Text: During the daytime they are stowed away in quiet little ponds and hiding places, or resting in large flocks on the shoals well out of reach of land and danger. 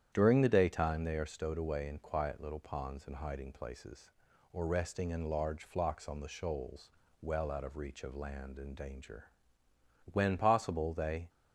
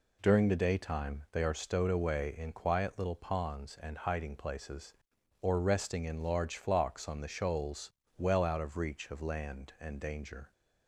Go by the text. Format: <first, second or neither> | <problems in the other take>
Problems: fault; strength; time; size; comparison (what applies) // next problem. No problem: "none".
second | starts louder than the rest; strong; until 1.1 s; 9.5 dB // pauses between "shoals" and "well"; slight; at 6.9 s; 0.32 s long; slight in the second // goes on to say "When possible they"; noticeable; from 10.1 s on; 1.1 s long